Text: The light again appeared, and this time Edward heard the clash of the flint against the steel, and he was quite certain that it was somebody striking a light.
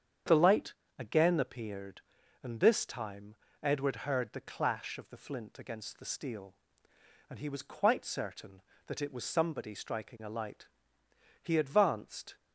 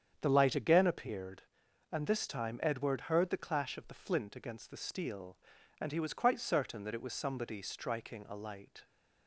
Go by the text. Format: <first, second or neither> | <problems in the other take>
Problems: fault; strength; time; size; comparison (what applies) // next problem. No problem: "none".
second | starts louder than the rest; strong; until 1.5 s; 8 dB; strong in the second // pauses between "light" and "again"; slight; at 0.7 s; 0.26 s long // pauses between "time" and "Edward"; slight; at 3.3 s; 0.28 s long // goes on to say "He advanced"; noticeable; from 11.4 s on; 0.94 s long